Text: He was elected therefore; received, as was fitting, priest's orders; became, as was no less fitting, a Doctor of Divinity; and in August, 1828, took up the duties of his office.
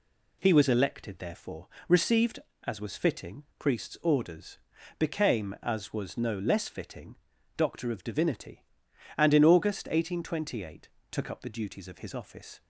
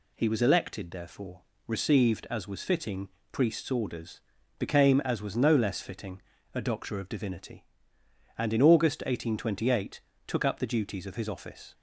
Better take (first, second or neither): second